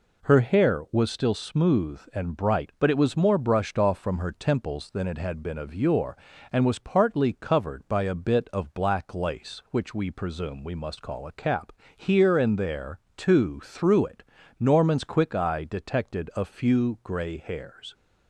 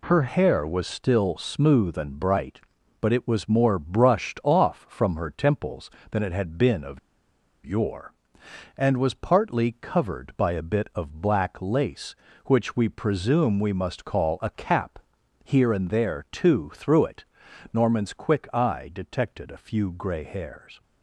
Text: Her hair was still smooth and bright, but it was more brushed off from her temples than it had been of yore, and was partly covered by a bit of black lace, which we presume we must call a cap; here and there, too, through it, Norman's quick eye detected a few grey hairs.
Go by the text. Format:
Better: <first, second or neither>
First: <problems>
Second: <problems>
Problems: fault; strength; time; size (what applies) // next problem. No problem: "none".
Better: first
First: none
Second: pauses between "of" and "yore"; noticeable; at 6.9 s; 0.64 s long